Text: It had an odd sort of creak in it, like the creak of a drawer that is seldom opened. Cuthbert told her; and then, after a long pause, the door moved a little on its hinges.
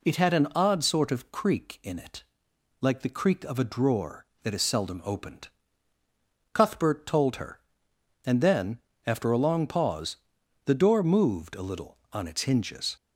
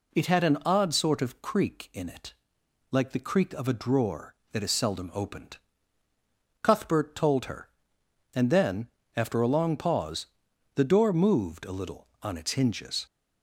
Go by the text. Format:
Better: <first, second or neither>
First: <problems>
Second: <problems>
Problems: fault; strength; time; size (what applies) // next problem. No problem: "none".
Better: neither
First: none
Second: none